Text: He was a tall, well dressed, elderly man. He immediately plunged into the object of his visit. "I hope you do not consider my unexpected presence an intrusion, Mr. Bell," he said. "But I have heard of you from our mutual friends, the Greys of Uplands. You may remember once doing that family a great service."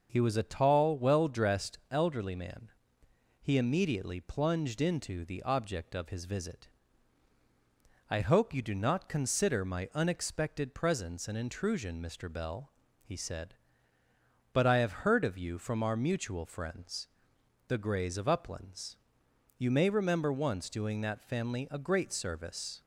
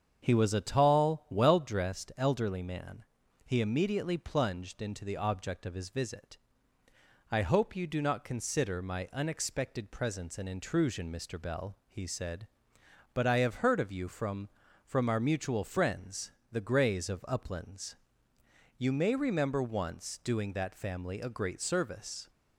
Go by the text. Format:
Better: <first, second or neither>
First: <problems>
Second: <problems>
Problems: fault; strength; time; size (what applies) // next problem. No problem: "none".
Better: first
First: none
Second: starts louder than the rest; strong; until 1.2 s; 7.5 dB // says "from" twice; at 14.8 s